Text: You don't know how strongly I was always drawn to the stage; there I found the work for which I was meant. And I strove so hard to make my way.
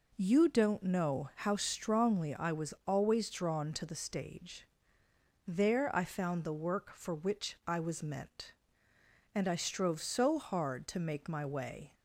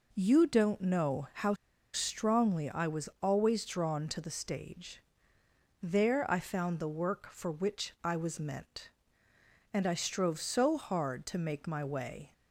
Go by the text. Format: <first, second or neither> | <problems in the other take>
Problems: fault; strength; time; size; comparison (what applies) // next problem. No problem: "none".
first | pauses between "how" and "strongly"; at 1.5 s; 0.40 s long